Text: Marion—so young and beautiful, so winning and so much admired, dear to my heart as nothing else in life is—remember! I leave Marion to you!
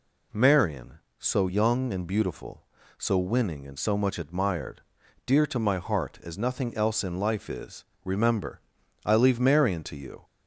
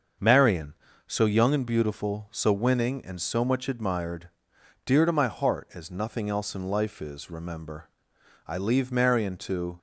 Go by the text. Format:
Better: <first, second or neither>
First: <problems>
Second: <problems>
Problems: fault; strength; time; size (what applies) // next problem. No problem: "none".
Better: first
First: none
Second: starts louder than the rest; until 1.5 s; 6.5 dB // stops before "you"; at 9.7 s